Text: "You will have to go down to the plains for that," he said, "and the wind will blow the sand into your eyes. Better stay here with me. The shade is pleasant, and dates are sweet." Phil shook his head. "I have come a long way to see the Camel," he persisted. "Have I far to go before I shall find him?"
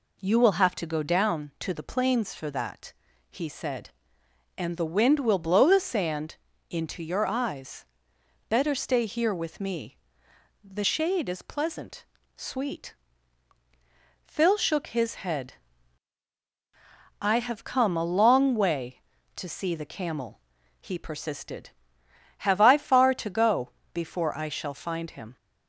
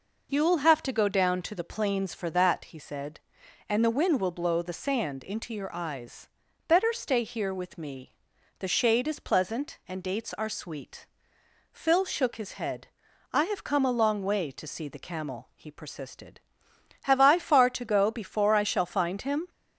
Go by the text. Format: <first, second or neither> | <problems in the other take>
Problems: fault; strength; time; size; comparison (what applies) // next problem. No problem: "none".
second | pauses between "sand" and "into"; slight; at 6.3 s; 0.34 s long // skips "and dates are"; at 12.1 s // pauses between "go" and "before"; slight; at 23.6 s; 0.24 s long